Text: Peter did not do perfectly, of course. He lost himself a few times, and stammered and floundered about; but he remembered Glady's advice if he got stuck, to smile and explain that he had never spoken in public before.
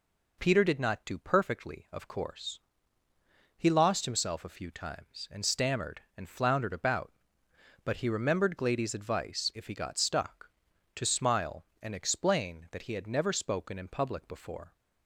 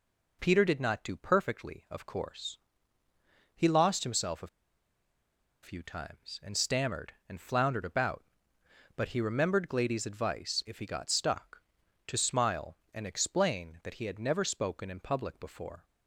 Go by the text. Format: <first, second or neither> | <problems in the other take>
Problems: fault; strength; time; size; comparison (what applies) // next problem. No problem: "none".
first | pauses between "a" and "few"; at 4.4 s; 1.1 s long